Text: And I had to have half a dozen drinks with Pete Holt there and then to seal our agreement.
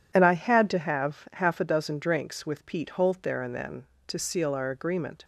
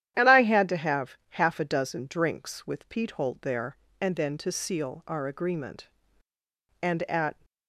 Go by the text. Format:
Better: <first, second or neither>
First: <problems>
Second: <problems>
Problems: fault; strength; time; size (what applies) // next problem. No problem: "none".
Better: first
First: none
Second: starts louder than the rest; strong; until 1.1 s; 11 dB // goes on to say "And at"; noticeable; from 6.8 s on; 0.64 s long